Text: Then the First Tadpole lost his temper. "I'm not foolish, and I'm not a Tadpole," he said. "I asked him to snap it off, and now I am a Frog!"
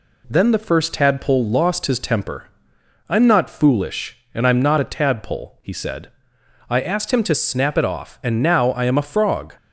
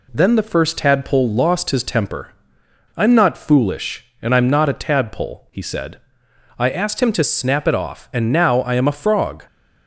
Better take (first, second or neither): neither